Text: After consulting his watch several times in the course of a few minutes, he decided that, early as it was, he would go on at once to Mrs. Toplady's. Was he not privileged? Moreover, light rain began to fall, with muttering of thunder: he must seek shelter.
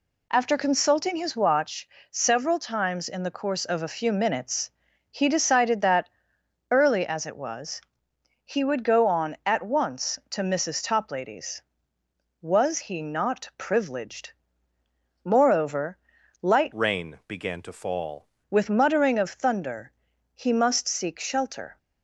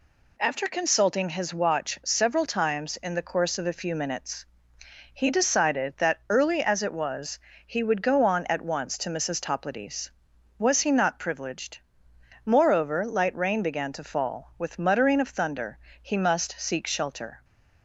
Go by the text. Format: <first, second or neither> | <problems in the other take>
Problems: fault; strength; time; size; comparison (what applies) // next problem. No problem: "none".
second | pauses between "watch" and "several"; slight; at 1.8 s; 0.22 s long // changes voice from "rain" to "fall"; from 16.7 to 18.2 s; 1.5 s long